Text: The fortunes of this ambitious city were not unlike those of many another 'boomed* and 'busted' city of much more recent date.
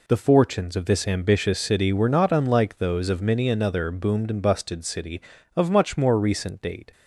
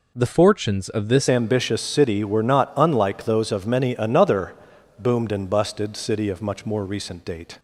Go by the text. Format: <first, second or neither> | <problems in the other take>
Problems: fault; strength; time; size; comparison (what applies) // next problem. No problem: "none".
first | changes voice at "ambitious"; from 1.2 s on; 6.3 s long // pauses between "another" and "boomed"; at 4.5 s; 0.42 s long